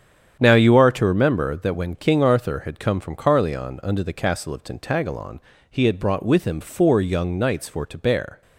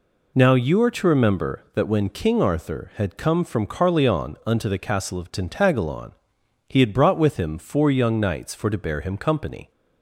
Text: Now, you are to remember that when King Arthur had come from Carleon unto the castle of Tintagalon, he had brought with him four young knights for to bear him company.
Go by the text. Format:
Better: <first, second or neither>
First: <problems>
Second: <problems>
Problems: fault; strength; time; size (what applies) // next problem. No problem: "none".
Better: second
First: starts louder than the rest; strong; until 1.4 s; 8.5 dB // stops before "him company"; at 8.4 s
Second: none